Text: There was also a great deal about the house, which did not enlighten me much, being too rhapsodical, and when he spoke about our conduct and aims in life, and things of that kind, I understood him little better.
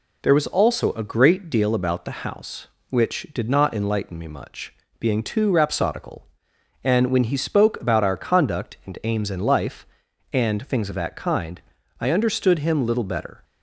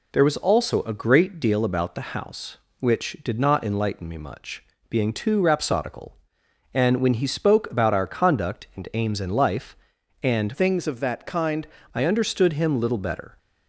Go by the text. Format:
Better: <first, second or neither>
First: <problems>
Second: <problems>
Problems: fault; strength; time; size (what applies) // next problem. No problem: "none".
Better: first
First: none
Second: changes voice from "things" to "kind"; from 10.5 to 11.6 s; 1.1 s long